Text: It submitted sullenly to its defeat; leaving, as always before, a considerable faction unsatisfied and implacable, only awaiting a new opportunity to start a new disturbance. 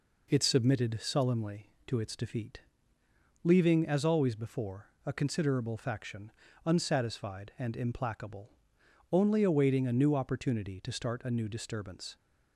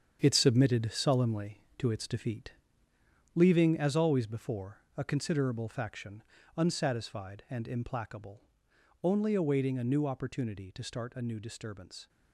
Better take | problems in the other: first | gets quieter; strong; throughout; 8.5 dB // pauses between "faction" and "unsatisfied"; slight; at 6.2 s; 0.36 s long; slight in the first

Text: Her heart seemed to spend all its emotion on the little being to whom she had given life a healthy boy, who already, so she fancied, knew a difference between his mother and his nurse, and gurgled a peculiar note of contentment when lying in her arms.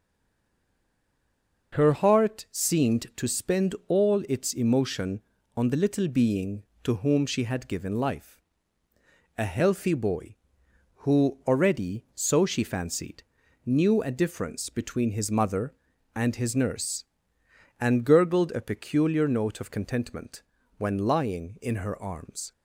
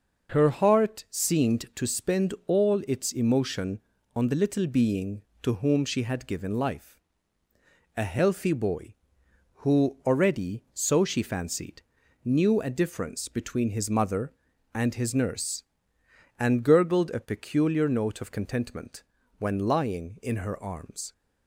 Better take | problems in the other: second | stays silent before the first word; noticeable; until 1.7 s; 1.7 s long // pauses between "life" and "a"; noticeable; at 8.4 s; 0.96 s long; noticeable in the second // pauses between "contentment" and "when"; slight; at 20.4 s; 0.36 s long; slight in the second

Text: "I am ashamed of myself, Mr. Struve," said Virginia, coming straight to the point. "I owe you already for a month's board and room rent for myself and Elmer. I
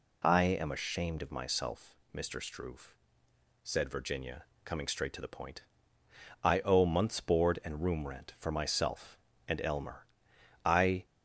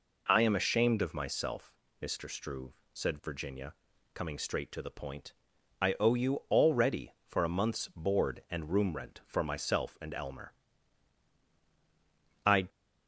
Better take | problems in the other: second | skips "you already for a"; at 6.8 s

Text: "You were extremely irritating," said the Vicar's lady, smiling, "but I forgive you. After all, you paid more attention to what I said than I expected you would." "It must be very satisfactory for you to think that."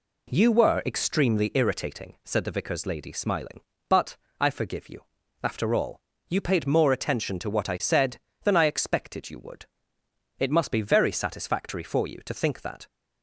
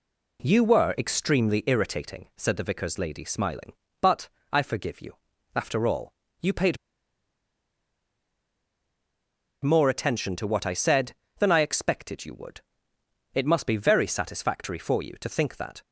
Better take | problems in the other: first | pauses between "but" and "I"; slight; at 4.2 s; 0.22 s long; slight in the first // pauses between "paid" and "more"; strong; at 6.7 s; 2.8 s long

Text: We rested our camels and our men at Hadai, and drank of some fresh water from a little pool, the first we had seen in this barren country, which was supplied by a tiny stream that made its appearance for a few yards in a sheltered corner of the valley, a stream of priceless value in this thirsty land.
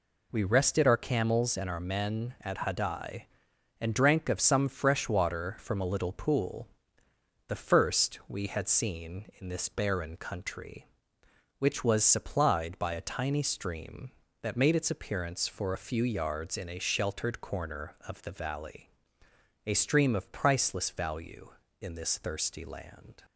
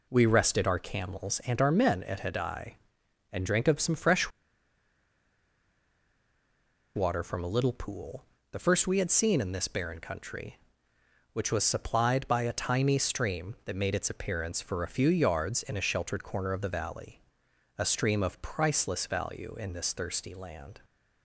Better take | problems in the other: first | pauses between "fresh" and "water"; strong; at 4.2 s; 2.6 s long

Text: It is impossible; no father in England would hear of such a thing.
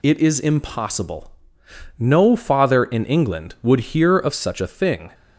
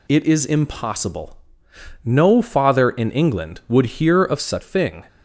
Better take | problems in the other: first | skips "a"; at 4.6 s

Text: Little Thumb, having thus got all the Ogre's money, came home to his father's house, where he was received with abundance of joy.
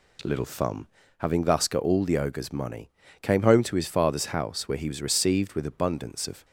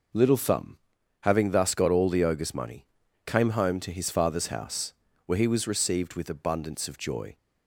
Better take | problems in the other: second | stops before "joy"; at 6.4 s

